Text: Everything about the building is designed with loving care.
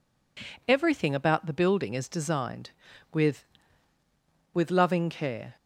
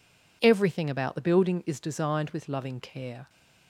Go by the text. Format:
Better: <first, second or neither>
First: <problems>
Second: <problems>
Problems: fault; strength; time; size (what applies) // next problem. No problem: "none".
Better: second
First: says "with" twice; at 4.5 s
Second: none